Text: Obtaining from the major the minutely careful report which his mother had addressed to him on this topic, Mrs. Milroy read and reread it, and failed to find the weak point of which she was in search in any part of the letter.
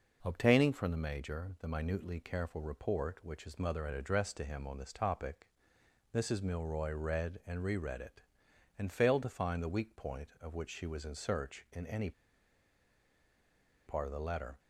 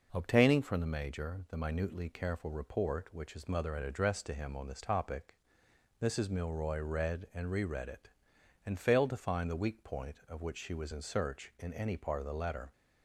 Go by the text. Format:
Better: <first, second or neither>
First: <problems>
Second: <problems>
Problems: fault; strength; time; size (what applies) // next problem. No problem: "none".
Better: second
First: pauses between "any" and "part"; strong; at 12.1 s; 1.7 s long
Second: none